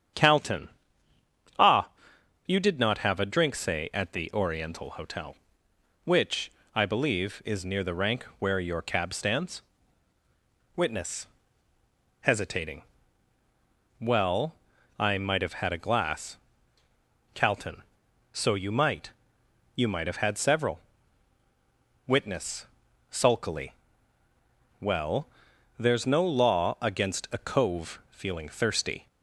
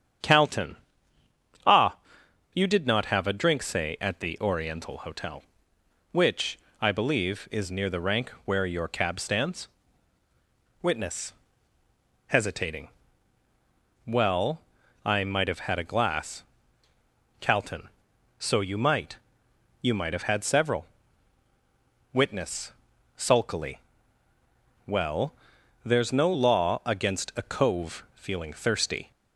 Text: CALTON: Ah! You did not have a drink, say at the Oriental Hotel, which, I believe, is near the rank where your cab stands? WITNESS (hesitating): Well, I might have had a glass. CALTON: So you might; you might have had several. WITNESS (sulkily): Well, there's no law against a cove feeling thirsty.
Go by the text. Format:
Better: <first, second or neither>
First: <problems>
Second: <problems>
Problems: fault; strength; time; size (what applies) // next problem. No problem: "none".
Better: neither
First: starts louder than the rest; strong; until 2.6 s; 8.5 dB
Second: starts louder than the rest; strong; until 2.6 s; 8.5 dB